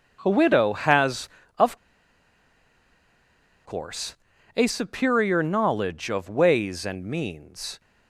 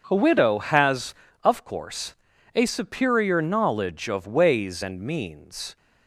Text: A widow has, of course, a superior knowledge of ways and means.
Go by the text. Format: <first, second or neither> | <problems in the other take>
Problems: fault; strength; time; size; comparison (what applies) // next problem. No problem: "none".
second | pauses between "of" and "course"; strong; at 1.7 s; 1.8 s long